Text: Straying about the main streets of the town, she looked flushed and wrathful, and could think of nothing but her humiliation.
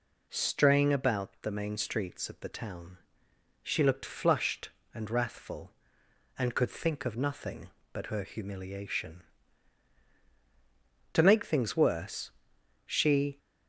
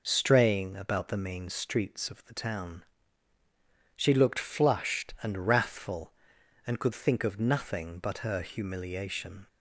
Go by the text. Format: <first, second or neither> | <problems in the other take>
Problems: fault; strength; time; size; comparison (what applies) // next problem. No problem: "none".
second | goes on to say "To make things worse she"; strong; from 11.1 s on; 2.2 s long